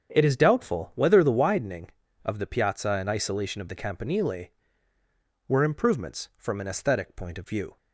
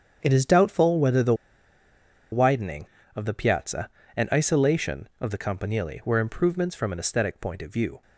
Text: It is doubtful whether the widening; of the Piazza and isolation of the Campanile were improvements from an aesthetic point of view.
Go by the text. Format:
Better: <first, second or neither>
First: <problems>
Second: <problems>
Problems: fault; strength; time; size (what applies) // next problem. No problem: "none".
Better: first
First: starts louder than the rest; strong; until 1.1 s; 7.5 dB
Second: starts louder than the rest; strong; until 1.2 s; 7.5 dB // pauses between "the" and "widening"; at 1.3 s; 0.98 s long